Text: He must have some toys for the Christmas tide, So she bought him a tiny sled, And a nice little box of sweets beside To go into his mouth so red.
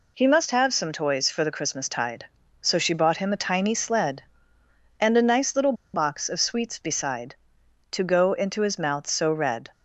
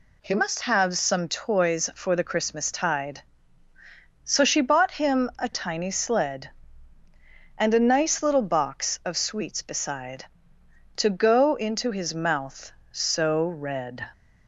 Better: second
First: pauses between "little" and "box"; slight; at 5.7 s; 0.20 s long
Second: none

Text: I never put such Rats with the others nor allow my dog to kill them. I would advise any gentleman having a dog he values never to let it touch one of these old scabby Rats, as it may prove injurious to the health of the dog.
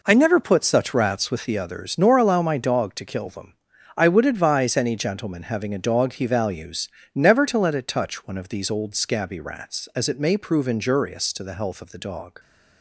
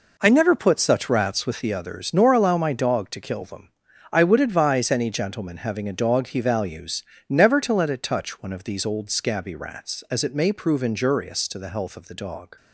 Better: neither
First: pauses between "values" and "never"; slight; at 6.8 s; 0.26 s long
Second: pauses between "values" and "never"; slight; at 7.0 s; 0.26 s long

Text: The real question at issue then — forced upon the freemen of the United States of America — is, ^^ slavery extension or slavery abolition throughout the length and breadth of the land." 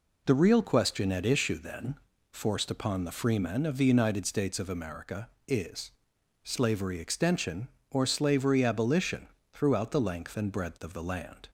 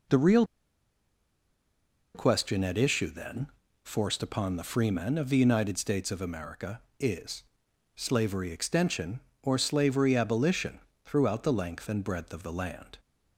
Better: first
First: pauses between "abolition" and "throughout"; slight; at 9.2 s; 0.26 s long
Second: pauses between "real" and "question"; strong; at 0.4 s; 1.7 s long // pauses between "abolition" and "throughout"; slight; at 10.8 s; 0.26 s long

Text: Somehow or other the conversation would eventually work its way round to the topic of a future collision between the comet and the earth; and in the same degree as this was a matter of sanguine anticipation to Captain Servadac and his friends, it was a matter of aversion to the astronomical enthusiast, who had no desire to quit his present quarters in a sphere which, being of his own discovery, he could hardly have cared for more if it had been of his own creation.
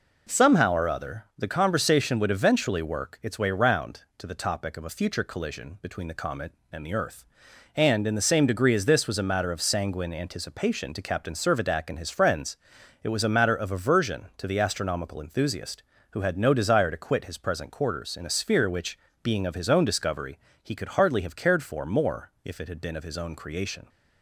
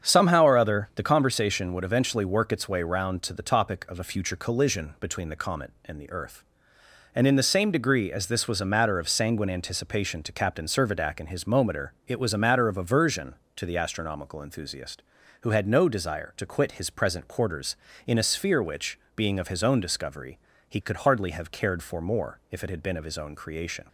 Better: first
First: none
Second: starts louder than the rest; strong; until 1.0 s; 7.5 dB // says "mometer" for "friends"; at 11.4 s

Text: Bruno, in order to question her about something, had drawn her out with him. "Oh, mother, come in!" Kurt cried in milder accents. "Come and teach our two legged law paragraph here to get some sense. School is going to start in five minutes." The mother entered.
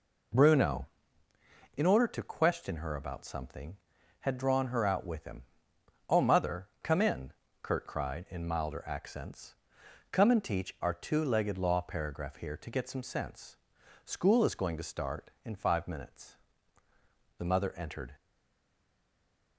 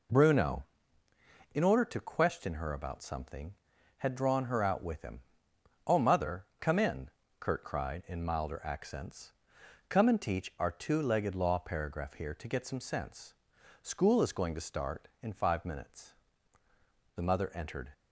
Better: second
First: stays silent after the last word; noticeable; from 18.1 s on; 1.4 s long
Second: none

